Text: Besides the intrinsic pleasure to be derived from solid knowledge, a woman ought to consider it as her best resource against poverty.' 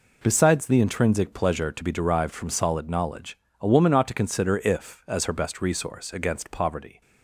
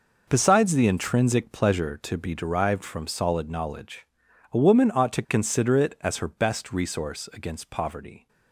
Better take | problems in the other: second | says "if" for "it"; at 4.5 s

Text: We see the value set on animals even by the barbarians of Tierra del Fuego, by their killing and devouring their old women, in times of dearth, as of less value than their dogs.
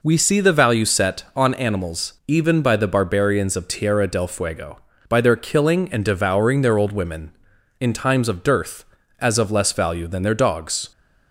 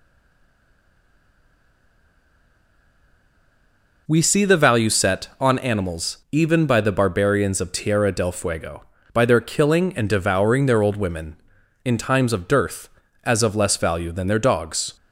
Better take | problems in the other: first | stays silent before the first word; strong; until 4.0 s; 4.0 s long

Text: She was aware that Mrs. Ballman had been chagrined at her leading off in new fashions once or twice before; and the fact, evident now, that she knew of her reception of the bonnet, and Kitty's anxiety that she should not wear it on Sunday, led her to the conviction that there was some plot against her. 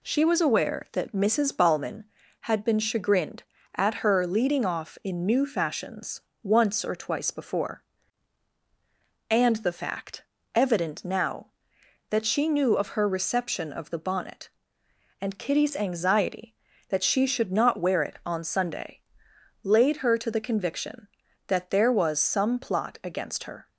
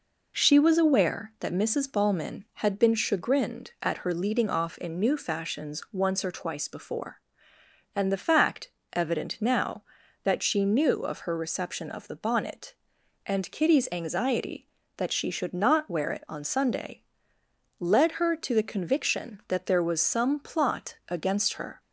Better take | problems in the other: second | pauses between "fashions" and "once"; slight; at 6.2 s; 0.22 s long // says "laid" for "led"; at 19.6 s

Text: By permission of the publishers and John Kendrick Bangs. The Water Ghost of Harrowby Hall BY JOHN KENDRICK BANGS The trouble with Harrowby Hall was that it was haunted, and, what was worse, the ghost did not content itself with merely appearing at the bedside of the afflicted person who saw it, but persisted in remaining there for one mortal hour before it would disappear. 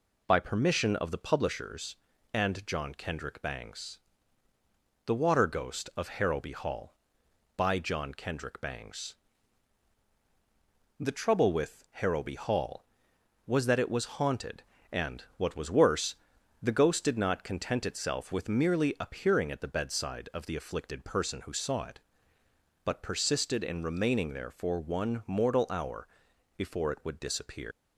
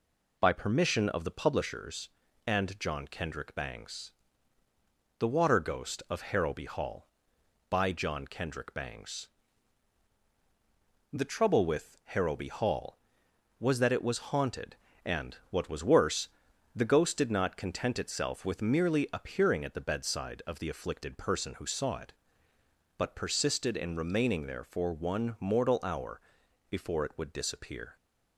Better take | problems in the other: second | pauses between "BANGS" and "The"; strong; at 9.1 s; 1.8 s long; strong in the second // pauses between "hour" and "before"; noticeable; at 26.0 s; 0.48 s long; noticeable in the second // leaves "disappear" unfinished; at 27.7 s; 110 ms

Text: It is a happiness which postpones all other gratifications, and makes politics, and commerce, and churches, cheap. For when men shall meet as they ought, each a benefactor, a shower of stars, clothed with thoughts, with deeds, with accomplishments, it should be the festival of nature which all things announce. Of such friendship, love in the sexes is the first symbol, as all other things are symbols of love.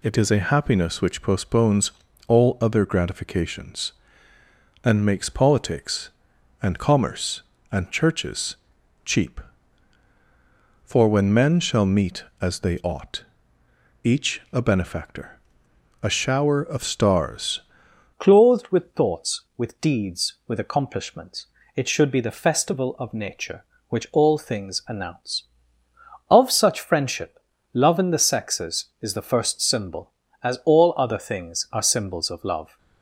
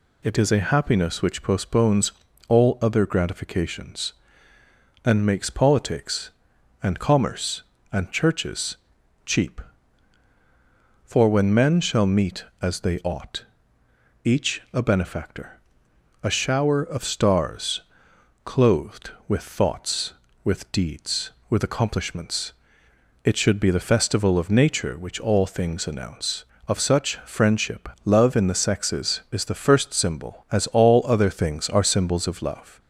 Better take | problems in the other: second | pauses between "postpones" and "all"; slight; at 1.9 s; 0.36 s long; slight in the second // changes voice at "clothed"; from 18.1 s on; 14.6 s long

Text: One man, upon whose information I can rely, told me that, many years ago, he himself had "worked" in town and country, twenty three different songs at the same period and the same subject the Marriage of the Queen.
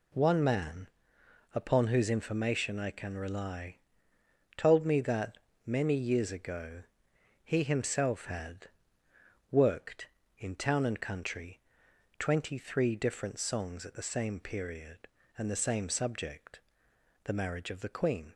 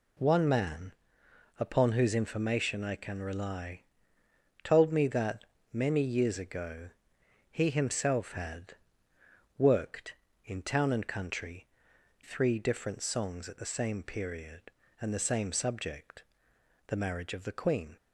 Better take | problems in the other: first | pauses between "had" and "worked"; noticeable; at 8.7 s; 0.84 s long; noticeable in the first // skips "twenty"; at 11.9 s // pauses between "subject" and "the"; noticeable; at 16.2 s; 0.64 s long; noticeable in the first

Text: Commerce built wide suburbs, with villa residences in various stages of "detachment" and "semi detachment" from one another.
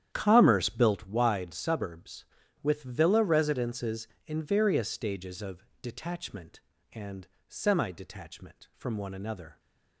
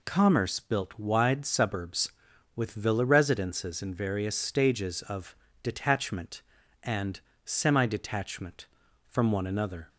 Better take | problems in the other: second | starts louder than the rest; strong; until 1.0 s; 10 dB // pauses between "of" and "detachment"; slight; at 5.6 s; 0.18 s long; slight in the second // pauses between "and" and "semi"; slight; at 7.2 s; 0.20 s long; slight in the second

